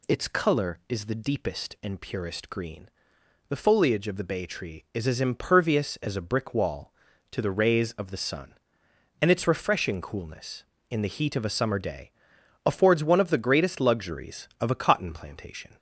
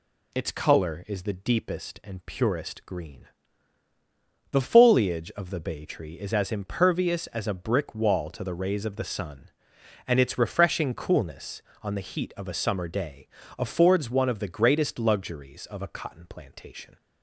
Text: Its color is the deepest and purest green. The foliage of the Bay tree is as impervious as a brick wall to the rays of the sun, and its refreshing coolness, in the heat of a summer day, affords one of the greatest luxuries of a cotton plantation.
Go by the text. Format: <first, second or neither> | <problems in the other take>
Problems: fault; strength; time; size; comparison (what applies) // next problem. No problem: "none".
first | says "on" for "in"; at 11.8 s